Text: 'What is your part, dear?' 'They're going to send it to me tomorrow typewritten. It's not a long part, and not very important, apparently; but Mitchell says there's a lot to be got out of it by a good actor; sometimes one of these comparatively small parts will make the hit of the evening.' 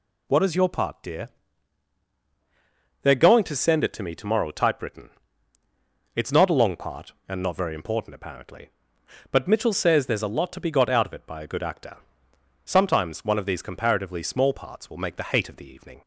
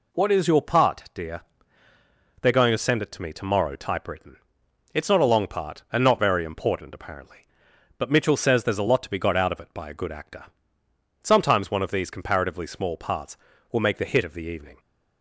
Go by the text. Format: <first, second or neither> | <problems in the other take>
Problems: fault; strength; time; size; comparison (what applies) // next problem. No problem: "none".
second | says "hate" for "hit"; at 15.2 s